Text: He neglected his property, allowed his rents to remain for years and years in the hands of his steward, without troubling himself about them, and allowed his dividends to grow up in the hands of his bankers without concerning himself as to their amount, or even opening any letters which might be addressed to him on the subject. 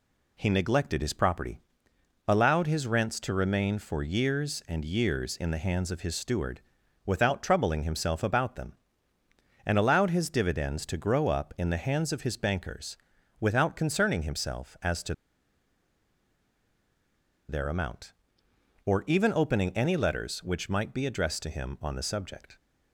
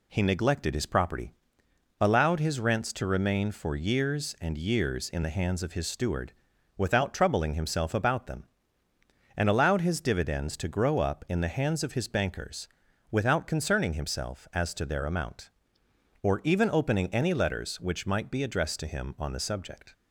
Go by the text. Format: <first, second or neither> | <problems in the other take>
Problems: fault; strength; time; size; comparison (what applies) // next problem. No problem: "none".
second | pauses between "bankers" and "without"; at 12.9 s; 0.44 s long; also in the second // pauses between "to" and "their"; strong; at 15.1 s; 2.3 s long